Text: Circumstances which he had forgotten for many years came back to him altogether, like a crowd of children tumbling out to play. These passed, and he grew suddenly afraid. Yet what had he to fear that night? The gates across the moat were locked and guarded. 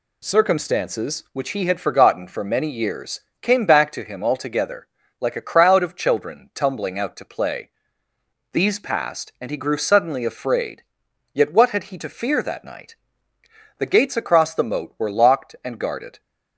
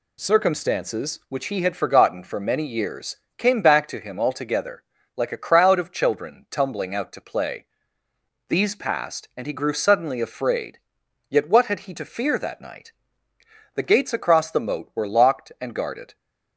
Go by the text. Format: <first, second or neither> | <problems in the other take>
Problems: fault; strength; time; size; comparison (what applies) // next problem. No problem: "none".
neither | pauses between "years" and "came"; slight; the same in both